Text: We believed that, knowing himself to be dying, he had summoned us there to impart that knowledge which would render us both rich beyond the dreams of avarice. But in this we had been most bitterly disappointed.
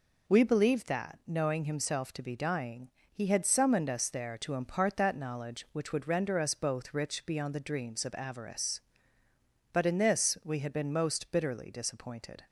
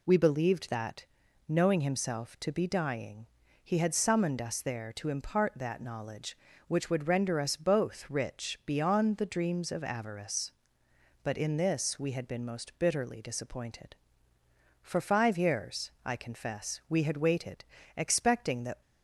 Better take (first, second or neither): first